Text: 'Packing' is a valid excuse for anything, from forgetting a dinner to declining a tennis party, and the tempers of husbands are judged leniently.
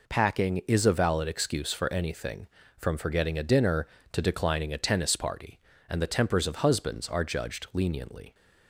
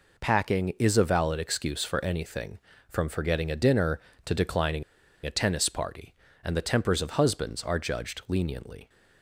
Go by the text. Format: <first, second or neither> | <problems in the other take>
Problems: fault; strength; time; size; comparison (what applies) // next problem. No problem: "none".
first | pauses between "declining" and "a"; at 4.8 s; 0.41 s long